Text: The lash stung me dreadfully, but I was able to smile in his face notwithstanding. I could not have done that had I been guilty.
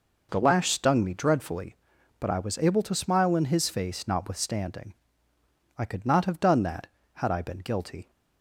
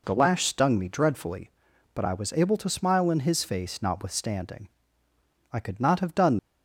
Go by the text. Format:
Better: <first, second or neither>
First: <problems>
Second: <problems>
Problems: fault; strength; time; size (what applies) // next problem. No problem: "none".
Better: first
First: none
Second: stops before "that had I been guilty"; at 6.3 s